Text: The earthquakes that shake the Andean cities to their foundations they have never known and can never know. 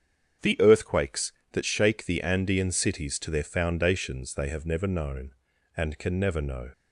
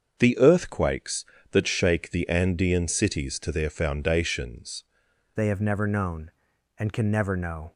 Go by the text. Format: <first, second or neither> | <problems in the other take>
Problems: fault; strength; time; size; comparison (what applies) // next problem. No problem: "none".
first | starts louder than the rest; until 1.2 s; 7 dB; strong in the first // changes voice at "they"; from 5.3 s on; 2.4 s long